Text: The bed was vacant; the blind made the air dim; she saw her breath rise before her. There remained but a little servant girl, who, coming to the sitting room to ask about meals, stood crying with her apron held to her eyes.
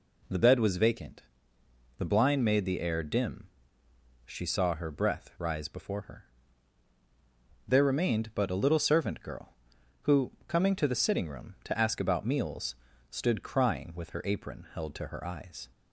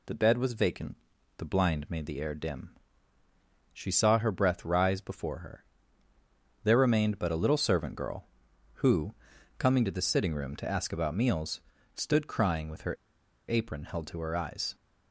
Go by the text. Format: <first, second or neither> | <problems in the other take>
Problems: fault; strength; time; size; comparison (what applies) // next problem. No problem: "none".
first | pauses between "her" and "apron"; noticeable; at 12.9 s; 0.54 s long